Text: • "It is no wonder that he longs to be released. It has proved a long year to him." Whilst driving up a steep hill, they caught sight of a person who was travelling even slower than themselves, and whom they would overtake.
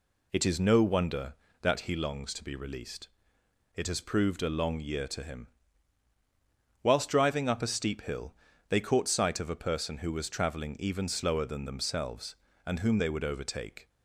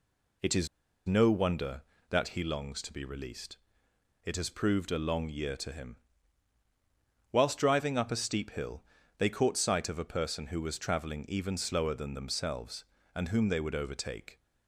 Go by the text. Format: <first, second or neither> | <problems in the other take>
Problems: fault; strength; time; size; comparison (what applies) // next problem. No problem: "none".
first | pauses between "is" and "no"; at 0.6 s; 0.39 s long